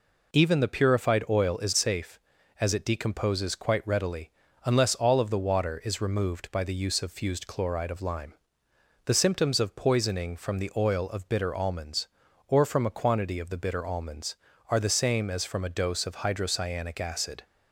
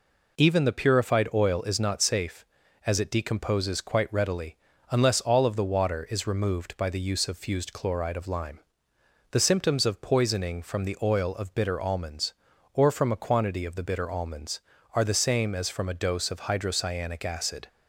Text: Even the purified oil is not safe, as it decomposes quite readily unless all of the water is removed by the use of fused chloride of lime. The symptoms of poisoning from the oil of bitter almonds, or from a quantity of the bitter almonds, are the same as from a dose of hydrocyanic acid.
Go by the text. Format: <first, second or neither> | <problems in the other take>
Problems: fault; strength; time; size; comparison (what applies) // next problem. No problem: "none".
second | skips "not"; at 1.7 s // pauses between "readily" and "unless"; slight; at 4.3 s; 0.34 s long; slight in the second